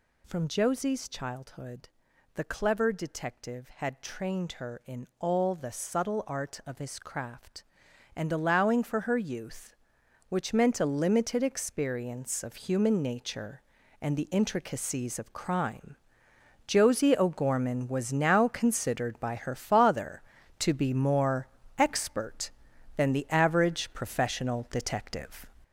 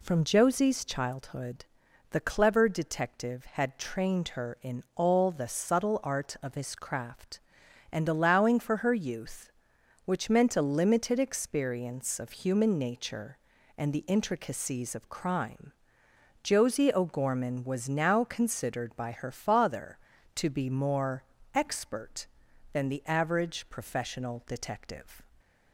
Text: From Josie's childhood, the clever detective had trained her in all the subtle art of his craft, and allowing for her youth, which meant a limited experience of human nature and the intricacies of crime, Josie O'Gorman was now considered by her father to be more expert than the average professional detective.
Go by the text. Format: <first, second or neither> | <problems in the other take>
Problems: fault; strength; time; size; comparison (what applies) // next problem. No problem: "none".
second | gets louder; noticeable; throughout; 6 dB // pauses between "more" and "expert"; slight; at 21.4 s; 0.32 s long; slight in the second